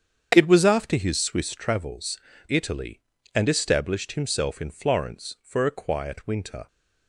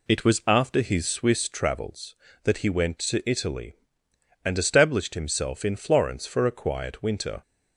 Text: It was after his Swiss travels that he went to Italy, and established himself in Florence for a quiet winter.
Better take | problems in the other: second | starts louder than the rest; strong; until 1.3 s; 8 dB // skips "that he went to"; at 2.3 s

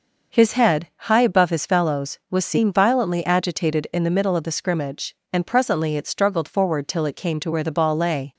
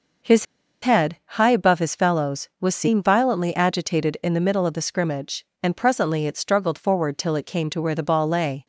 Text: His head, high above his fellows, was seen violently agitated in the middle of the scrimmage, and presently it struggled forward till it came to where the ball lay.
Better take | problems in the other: first | pauses between "His" and "head"; at 0.4 s; 0.38 s long

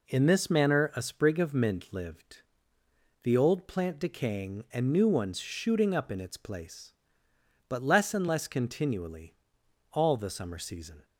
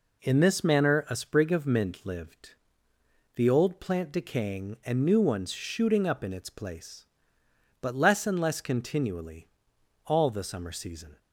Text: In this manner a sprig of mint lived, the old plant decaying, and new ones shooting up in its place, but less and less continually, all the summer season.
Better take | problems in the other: neither | none

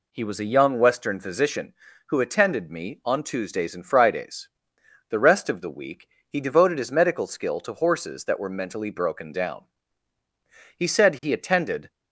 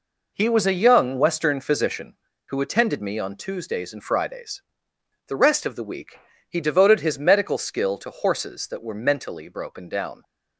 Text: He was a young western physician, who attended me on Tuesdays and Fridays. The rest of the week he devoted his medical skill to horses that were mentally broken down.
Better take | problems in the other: second | pauses between "week" and "he"; slight; at 6.0 s; 0.20 s long; slight in the second // goes on to say "He said he attended"; noticeable; from 10.7 s on; 1.1 s long

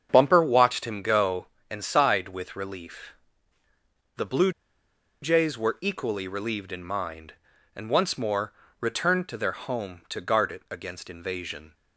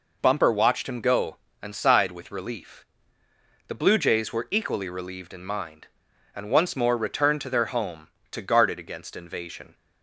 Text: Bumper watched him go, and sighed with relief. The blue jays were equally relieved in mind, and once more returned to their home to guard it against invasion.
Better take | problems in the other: second | starts louder than the rest; strong; until 1.1 s; 7.5 dB // pauses between "blue" and "jays"; noticeable; at 4.5 s; 0.71 s long // pauses between "more" and "returned"; slight; at 8.5 s; 0.26 s long

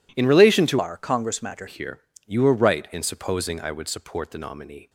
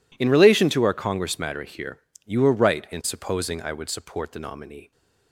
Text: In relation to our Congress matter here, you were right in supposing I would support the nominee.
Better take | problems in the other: second | changes voice from "our" to "matter"; from 0.7 to 1.6 s; 0.9 s long

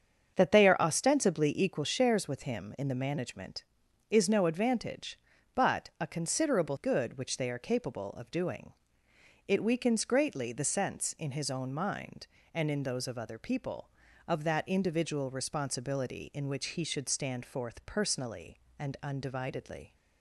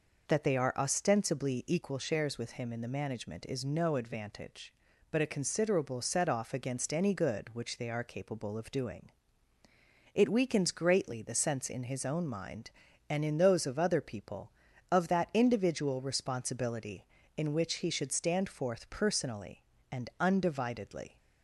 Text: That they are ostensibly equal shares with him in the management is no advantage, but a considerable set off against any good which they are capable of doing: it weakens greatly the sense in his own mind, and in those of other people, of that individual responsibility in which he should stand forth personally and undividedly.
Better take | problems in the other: second | starts louder than the rest; strong; until 1.3 s; 7 dB // skips "set off against any"; at 6.7 s

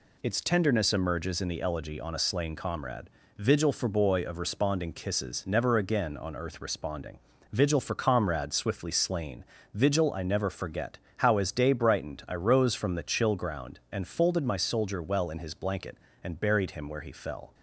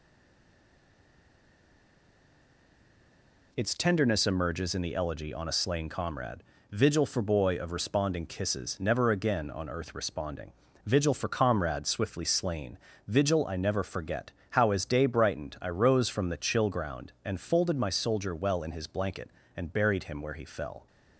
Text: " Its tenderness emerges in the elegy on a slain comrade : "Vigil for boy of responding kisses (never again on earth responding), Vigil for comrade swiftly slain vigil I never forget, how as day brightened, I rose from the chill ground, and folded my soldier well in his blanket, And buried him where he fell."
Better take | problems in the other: first | stays silent before the first word; strong; until 3.5 s; 3.5 s long // pauses between "slain" and "vigil"; slight; at 12.7 s; 0.28 s long; slight in the first

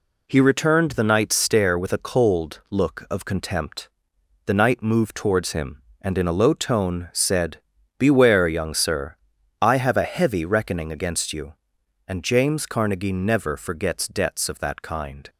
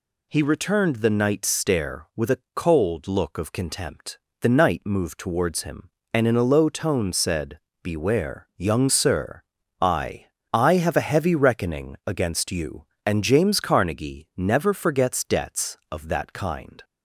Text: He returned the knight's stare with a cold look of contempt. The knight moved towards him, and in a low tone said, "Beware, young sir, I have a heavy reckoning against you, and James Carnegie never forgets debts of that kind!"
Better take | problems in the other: first | pauses between "a" and "cold"; slight; at 2.3 s; 0.16 s long // says "I" twice; at 10.5 s

